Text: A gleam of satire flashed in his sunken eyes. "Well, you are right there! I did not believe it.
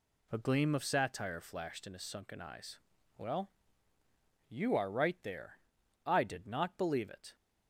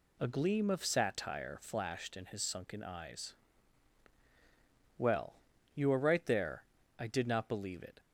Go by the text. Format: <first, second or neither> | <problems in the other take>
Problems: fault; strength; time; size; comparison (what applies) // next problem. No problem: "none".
neither | none